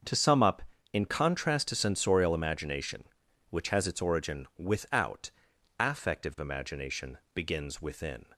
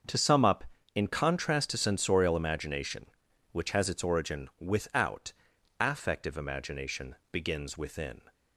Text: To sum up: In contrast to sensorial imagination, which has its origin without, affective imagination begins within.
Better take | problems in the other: neither | starts louder than the rest; the same in both // pauses between "imagination" and "begins"; slight; the same in both

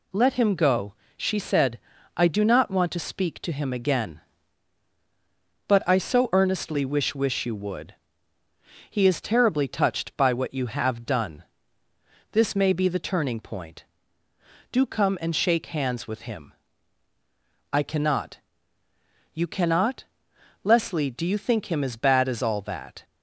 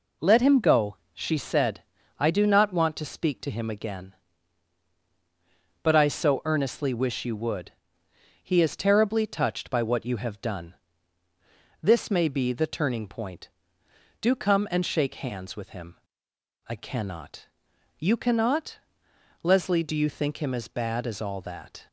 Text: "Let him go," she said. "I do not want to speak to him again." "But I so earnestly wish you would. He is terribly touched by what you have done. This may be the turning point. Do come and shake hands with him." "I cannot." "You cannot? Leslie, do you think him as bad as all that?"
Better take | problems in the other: second | says "wish" twice; at 7.1 s

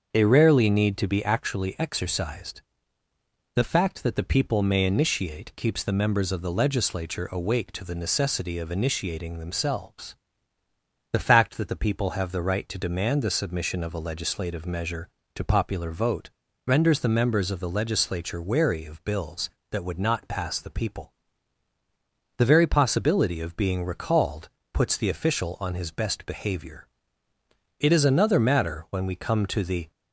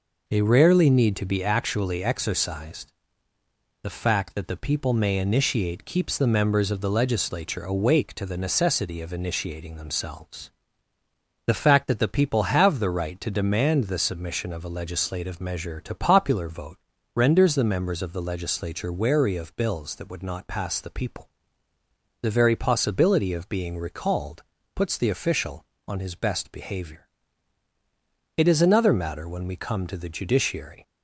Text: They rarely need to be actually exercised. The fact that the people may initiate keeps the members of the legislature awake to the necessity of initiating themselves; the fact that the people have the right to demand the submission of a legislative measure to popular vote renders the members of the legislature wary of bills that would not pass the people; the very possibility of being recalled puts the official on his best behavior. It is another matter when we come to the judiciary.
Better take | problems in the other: second | starts louder than the rest; until 1.1 s; 6.5 dB // pauses between "vote" and "renders"; slight; at 16.3 s; 0.36 s long; slight in the second // pauses between "recalled" and "puts"; slight; at 24.4 s; 0.24 s long; slight in the second // stops before "judiciary"; at 29.9 s

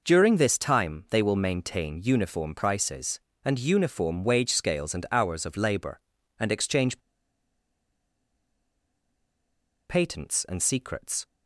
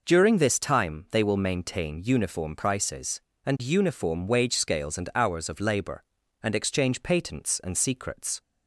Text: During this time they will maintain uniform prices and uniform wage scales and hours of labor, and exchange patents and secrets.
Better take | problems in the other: second | pauses between "exchange" and "patents"; strong; at 6.9 s; 2.9 s long

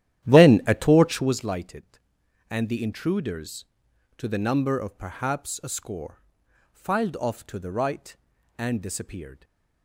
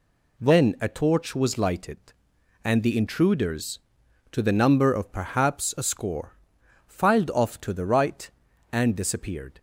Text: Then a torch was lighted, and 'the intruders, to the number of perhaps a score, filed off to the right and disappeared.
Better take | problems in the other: second | starts louder than the rest; strong; until 1.4 s; 12 dB // stays silent after the last word; slight; from 9.3 s on; 0.5 s long

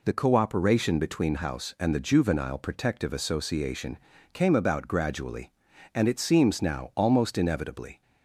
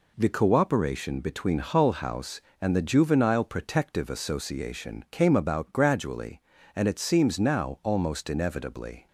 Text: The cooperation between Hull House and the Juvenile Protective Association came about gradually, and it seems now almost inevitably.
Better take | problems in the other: second | skips "Hull"; at 1.3 s // pauses between "Association" and "came"; slight; at 3.9 s; 0.36 s long

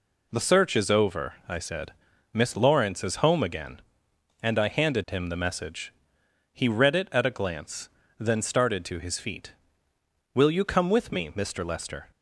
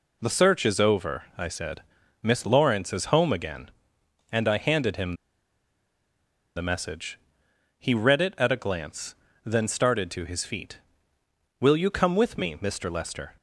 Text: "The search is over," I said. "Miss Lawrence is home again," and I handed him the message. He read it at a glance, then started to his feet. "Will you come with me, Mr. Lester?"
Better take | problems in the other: first | pauses between "him" and "the"; strong; at 5.1 s; 1.4 s long

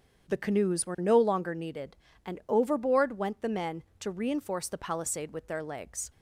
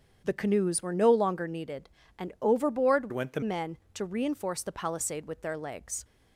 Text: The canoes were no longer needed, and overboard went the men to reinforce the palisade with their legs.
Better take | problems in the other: first | starts louder than the rest; strong; until 1.2 s; 8 dB; strong in the first // changes voice from "went" to "the"; from 3.1 to 3.4 s; 0.3 s long

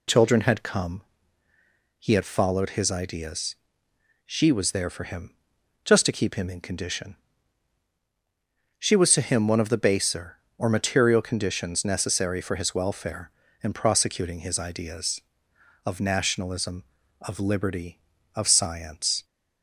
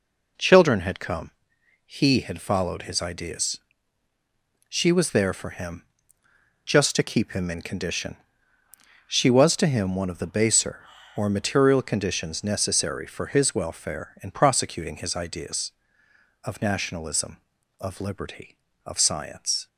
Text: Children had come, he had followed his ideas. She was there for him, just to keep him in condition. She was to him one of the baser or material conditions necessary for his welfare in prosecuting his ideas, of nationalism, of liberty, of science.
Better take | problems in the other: neither | none

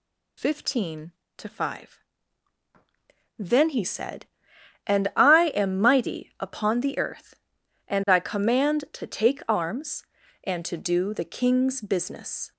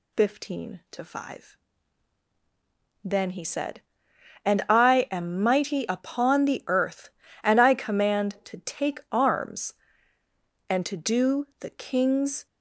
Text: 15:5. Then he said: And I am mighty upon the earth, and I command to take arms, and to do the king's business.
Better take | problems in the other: first | stops before "business"; at 12.4 s

